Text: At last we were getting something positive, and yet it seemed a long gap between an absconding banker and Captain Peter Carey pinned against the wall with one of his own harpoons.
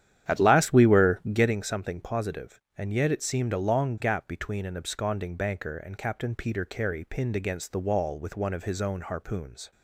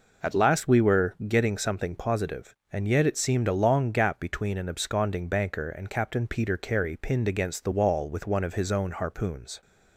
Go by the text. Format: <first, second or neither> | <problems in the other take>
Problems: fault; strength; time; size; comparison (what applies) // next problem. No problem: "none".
second | starts louder than the rest; strong; until 1.6 s; 10 dB